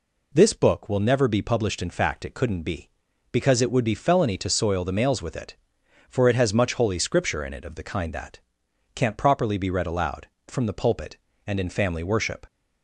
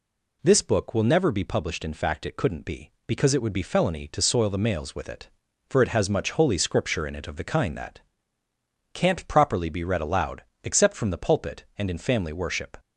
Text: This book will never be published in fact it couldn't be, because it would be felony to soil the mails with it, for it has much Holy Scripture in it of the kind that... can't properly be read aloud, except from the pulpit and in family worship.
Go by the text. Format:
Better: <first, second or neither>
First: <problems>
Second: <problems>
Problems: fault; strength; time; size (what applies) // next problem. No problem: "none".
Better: second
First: skips "except"; at 10.3 s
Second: none